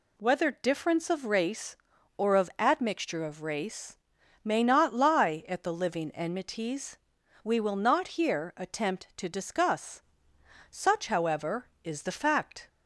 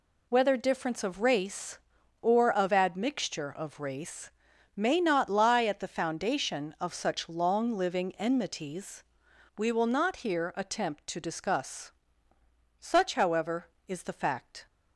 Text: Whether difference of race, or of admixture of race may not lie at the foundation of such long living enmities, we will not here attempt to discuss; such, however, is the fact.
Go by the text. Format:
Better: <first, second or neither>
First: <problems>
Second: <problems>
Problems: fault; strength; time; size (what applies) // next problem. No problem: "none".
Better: second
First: pauses between "race" and "may"; noticeable; at 3.9 s; 0.48 s long // skips "foundation of such long"; at 5.7 s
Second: pauses between "race" and "may"; noticeable; at 4.2 s; 0.46 s long